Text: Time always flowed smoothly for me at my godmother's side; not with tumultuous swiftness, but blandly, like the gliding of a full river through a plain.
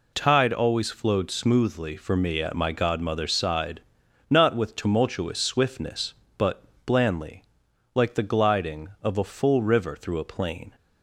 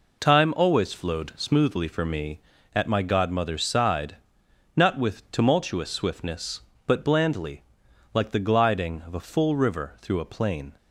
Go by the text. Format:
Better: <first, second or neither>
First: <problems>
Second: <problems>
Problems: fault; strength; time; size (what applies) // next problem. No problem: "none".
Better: second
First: says "Tide" for "Time"; at 0.1 s // pauses between "but" and "blandly"; slight; at 6.6 s; 0.22 s long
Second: none